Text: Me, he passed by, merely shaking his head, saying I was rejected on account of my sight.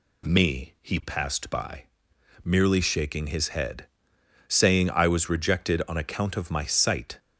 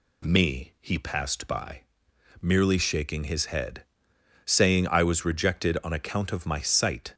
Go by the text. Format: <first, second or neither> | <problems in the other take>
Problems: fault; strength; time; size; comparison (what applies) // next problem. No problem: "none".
neither | none